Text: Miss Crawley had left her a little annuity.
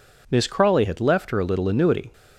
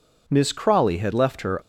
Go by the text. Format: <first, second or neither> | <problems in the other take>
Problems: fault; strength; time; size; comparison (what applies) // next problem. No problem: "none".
first | stops before "a little annuity"; at 1.5 s